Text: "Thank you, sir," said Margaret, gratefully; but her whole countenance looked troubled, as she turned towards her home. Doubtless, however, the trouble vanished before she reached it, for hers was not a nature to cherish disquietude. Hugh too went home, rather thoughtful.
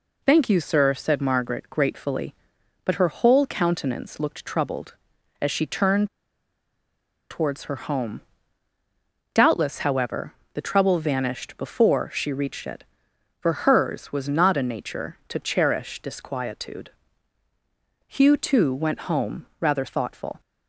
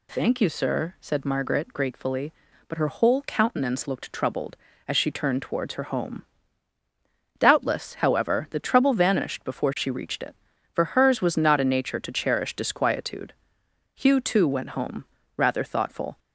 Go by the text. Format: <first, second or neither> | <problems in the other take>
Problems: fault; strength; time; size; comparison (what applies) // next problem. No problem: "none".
second | pauses between "turned" and "towards"; at 6.0 s; 1.2 s long